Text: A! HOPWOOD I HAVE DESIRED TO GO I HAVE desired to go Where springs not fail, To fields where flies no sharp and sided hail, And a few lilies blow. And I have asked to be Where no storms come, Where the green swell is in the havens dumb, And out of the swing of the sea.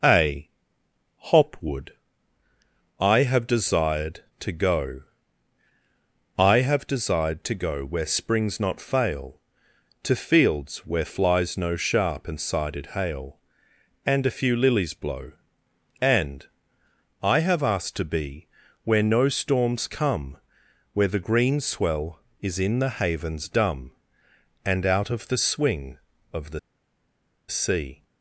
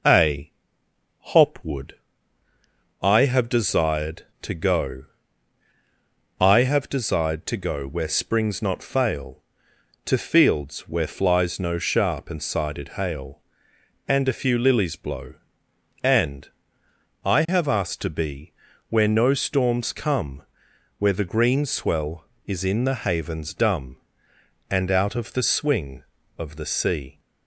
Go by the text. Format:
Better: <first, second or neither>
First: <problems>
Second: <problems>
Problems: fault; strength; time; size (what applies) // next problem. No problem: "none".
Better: second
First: pauses between "HOPWOOD" and "I"; at 1.9 s; 1.0 s long // pauses between "GO" and "I"; strong; at 5.0 s; 1.3 s long // pauses between "And" and "I"; noticeable; at 16.4 s; 0.76 s long // pauses between "be" and "Where"; at 18.4 s; 0.38 s long // pauses between "the" and "sea"; noticeable; at 26.5 s; 0.89 s long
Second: pauses between "HOPWOOD" and "I"; at 1.9 s; 1.0 s long // pauses between "GO" and "I"; strong; at 5.0 s; 1.3 s long // pauses between "And" and "I"; noticeable; at 16.4 s; 0.76 s long // pauses between "be" and "Where"; at 18.5 s; 0.38 s long